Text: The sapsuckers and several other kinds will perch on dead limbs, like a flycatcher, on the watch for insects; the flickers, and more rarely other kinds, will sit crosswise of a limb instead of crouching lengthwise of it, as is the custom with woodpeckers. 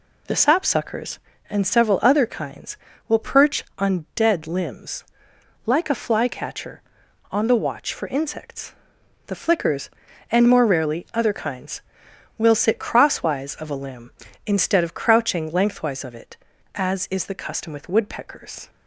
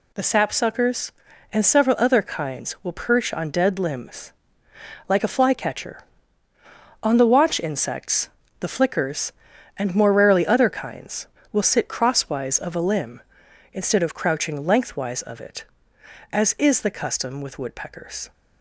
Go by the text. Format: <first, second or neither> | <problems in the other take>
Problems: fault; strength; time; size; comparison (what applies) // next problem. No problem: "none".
first | skips "for"; at 7.6 s